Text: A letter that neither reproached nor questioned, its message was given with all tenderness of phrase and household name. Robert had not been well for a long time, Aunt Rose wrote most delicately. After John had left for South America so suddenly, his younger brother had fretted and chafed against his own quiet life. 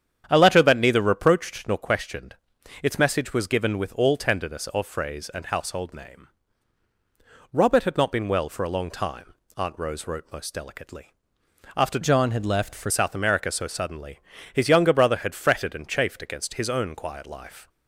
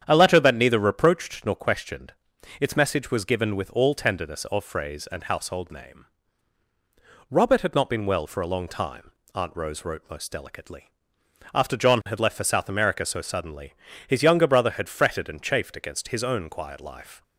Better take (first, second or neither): second